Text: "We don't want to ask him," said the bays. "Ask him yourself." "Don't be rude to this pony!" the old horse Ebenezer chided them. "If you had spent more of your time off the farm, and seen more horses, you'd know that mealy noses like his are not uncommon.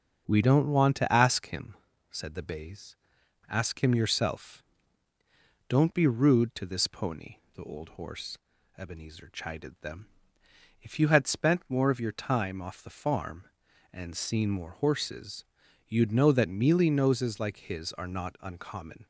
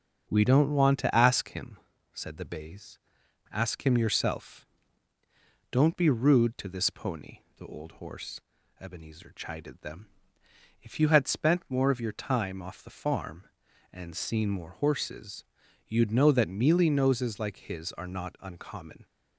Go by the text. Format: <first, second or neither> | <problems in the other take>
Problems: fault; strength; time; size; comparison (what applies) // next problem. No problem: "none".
neither | starts louder than the rest; the same in both // pauses between "horse" and "Ebenezer"; slight; the same in both